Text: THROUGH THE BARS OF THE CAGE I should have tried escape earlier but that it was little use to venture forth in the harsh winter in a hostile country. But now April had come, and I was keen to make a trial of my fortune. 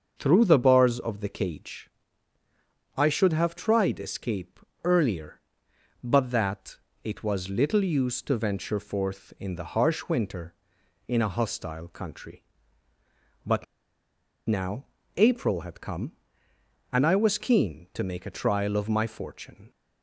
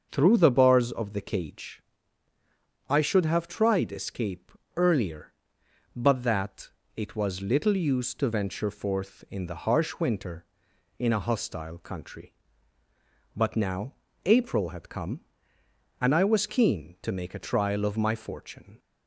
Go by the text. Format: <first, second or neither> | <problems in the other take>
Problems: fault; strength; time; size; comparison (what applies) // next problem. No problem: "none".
second | starts louder than the rest; until 1.1 s; 6.5 dB; also in the second // pauses between "CAGE" and "I"; at 1.9 s; 1.0 s long; also in the second // pauses between "escape" and "earlier"; slight; at 4.5 s; 0.24 s long; slight in the second // pauses between "that" and "it"; slight; at 6.7 s; 0.26 s long; slight in the second // pauses between "But" and "now"; noticeable; at 13.6 s; 0.83 s long // pauses between "now" and "April"; slight; at 14.8 s; 0.30 s long; slight in the second